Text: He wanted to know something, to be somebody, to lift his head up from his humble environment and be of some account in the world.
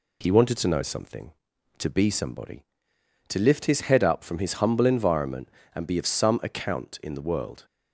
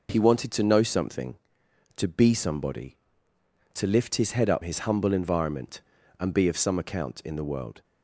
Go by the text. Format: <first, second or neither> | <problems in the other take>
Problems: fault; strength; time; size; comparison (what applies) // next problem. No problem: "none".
first | skips "from"; at 4.6 s